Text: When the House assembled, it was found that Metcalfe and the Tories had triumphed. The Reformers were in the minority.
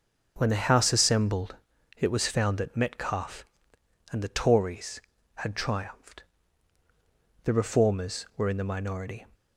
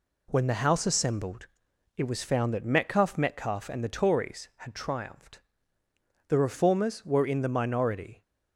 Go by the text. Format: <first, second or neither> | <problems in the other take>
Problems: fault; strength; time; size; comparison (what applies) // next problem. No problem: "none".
first | says "Metcalfe" twice; at 3.1 s